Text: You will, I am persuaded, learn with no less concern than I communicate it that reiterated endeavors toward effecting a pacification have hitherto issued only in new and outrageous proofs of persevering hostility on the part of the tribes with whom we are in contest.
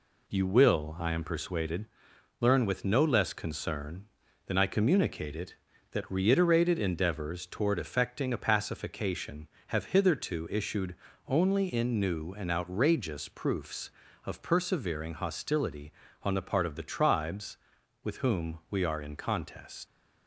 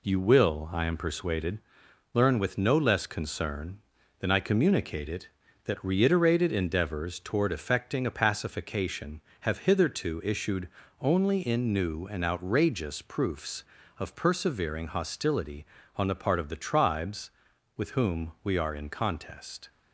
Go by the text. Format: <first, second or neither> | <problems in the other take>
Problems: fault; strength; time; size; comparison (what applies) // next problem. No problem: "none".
second | pauses between "issued" and "only"; slight; at 10.9 s; 0.34 s long; slight in the second // leaves "contest" unfinished; at 19.8 s; 80 ms